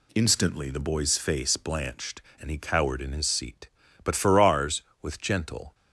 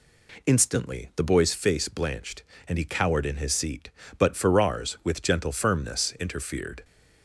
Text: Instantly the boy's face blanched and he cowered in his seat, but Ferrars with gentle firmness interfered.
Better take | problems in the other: second | stops before "firmness interfered"; at 5.7 s

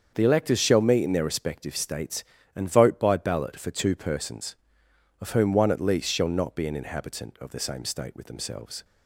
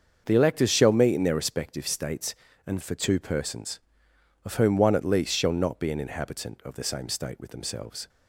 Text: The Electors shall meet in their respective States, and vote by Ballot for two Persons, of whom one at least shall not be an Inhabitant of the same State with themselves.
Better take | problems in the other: first | starts louder than the rest; until 1.2 s; 6.5 dB; also in the first // skips "vote by Ballot"; at 2.8 s

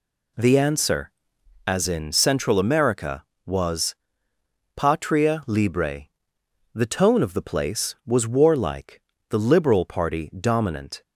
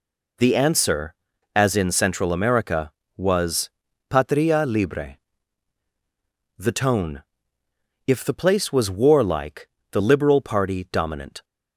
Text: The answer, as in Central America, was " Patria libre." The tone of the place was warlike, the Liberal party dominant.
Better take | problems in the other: first | says "if" for "of"; at 8.0 s

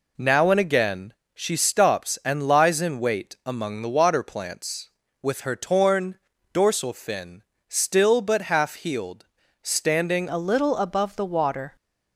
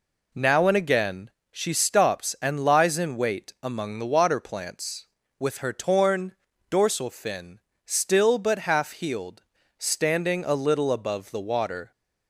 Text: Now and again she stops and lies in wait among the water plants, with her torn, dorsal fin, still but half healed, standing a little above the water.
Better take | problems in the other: second | pauses between "again" and "she"; slight; at 1.1 s; 0.22 s long; slight in the second // changes voice at "a"; from 10.2 s on; 1.5 s long

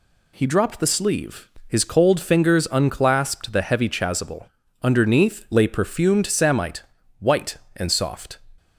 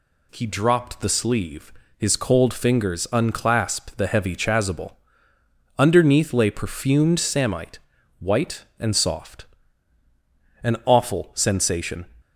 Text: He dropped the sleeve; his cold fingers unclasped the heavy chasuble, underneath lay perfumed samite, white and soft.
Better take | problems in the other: first | goes on to say "An awful sensation"; from 10.6 s on; 1.4 s long

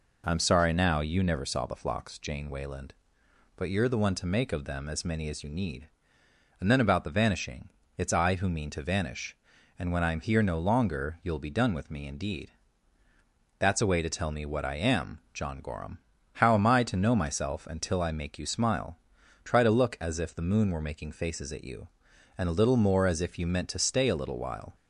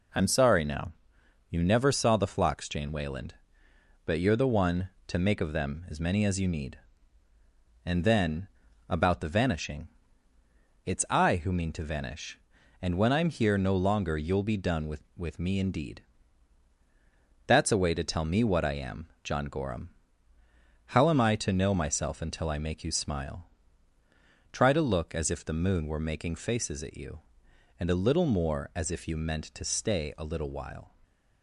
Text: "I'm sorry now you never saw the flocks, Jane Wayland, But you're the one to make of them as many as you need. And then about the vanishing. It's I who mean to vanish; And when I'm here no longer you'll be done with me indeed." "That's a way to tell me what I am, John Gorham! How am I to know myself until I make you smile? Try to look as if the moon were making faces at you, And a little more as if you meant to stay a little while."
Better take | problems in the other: first | pauses between "now" and "you"; noticeable; at 0.9 s; 0.60 s long // pauses between "then" and "about"; at 8.4 s; 0.42 s long // says "with" twice; at 15.1 s

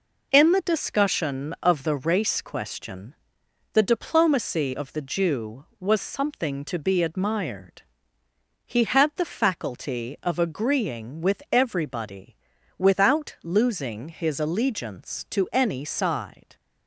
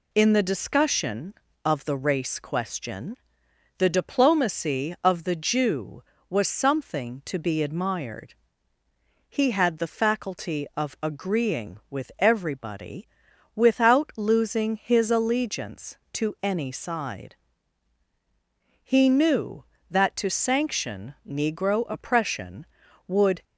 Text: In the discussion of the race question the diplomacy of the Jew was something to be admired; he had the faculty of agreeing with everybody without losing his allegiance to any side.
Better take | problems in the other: first | pauses between "question" and "the"; noticeable; at 3.1 s; 0.62 s long; noticeable in the first // pauses between "everybody" and "without"; noticeable; at 13.0 s; 0.48 s long; also in the first // goes on to say "He knew that to sanction Negro oppression would"; strong; from 18.8 s on; 4.6 s long

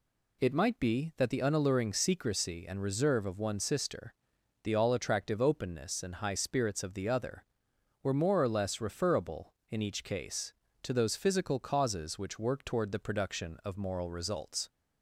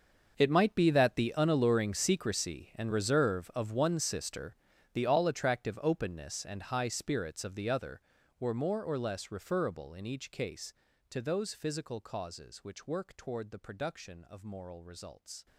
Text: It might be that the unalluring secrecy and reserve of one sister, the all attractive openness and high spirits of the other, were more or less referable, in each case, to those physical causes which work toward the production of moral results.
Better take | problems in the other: first | gets quieter; strong; throughout; 17.5 dB

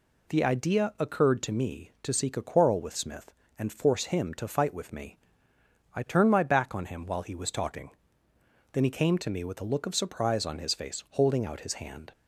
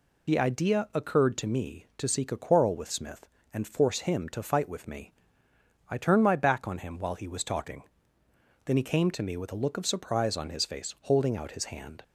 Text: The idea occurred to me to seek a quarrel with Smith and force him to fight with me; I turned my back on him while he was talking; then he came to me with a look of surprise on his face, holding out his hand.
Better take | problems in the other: first | loses the start of "The"; at 0.2 s; 30 ms

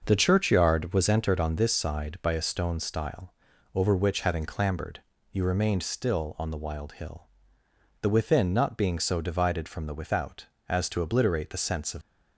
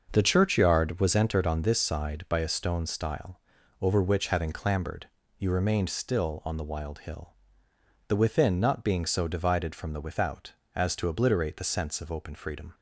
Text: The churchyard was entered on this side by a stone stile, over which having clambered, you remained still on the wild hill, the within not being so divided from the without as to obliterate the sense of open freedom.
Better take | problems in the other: second | starts louder than the rest; noticeable; until 1.0 s; 6 dB; noticeable in the second // stops before "open freedom"; at 12.0 s

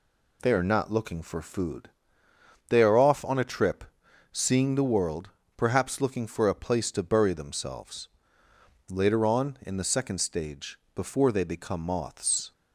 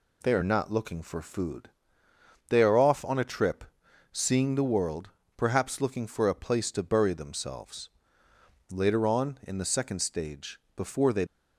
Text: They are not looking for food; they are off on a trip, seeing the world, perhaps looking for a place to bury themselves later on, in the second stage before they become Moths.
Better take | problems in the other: first | pauses between "themselves" and "later"; noticeable; at 7.8 s; 0.82 s long; noticeable in the first // pauses between "stage" and "before"; slight; at 10.5 s; 0.16 s long; slight in the first // stops before "become Moths"; at 11.2 s

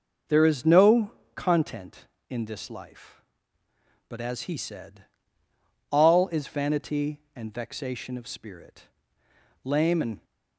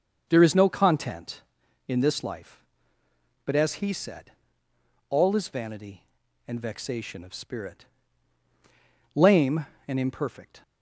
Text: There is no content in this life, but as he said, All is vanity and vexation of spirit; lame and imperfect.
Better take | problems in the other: second | starts louder than the rest; noticeable; until 1.5 s; 6 dB; also in the second // pauses between "no" and "content"; slight; at 1.1 s; 0.24 s long // stops before "imperfect"; at 10.2 s

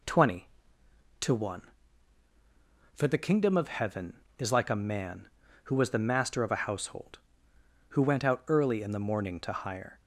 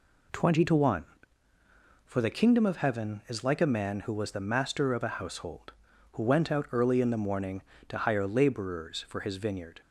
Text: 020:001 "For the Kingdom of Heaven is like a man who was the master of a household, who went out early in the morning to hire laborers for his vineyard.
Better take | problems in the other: second | stops before "laborers for his vineyard"; at 10.0 s

